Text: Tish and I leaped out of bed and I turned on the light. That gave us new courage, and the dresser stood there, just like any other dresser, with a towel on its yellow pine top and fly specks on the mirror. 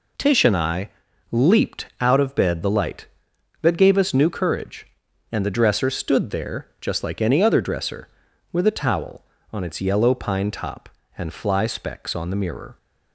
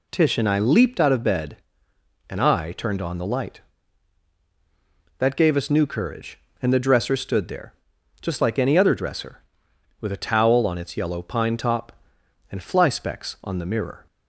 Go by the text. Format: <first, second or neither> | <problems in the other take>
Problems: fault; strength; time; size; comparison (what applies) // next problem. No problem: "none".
second | pauses between "I" and "leaped"; at 0.8 s; 0.42 s long // skips "and I turned on"; at 2.6 s